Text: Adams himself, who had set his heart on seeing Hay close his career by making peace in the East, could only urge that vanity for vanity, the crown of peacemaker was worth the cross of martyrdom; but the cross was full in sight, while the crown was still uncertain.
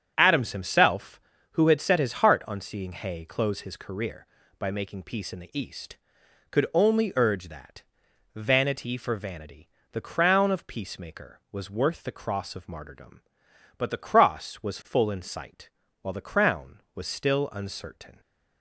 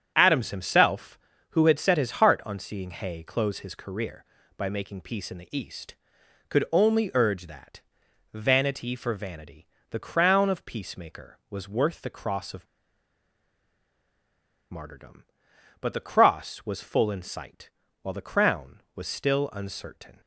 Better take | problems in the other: first | starts louder than the rest; strong; until 1.1 s; 7 dB; strong in the first // pauses between "that" and "vanity"; noticeable; at 7.8 s; 0.52 s long; noticeable in the first // pauses between "of" and "martyrdom"; strong; at 12.6 s; 2.0 s long

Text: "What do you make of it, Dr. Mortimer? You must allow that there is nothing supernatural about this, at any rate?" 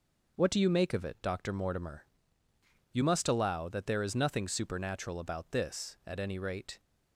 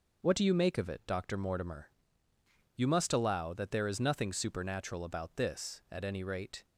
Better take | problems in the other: neither | none

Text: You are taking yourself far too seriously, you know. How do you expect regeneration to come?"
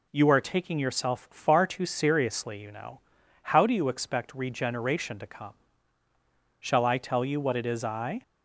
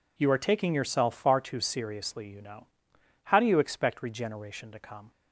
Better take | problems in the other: second | goes on to say "Shall I tell you what it is I"; from 6.5 s on; 1.6 s long

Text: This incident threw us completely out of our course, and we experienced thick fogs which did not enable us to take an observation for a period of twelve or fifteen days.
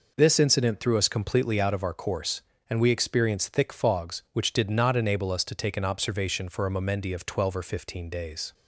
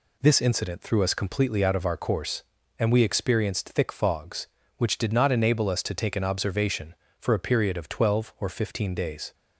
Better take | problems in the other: second | says "momendi" for "period"; at 6.7 s

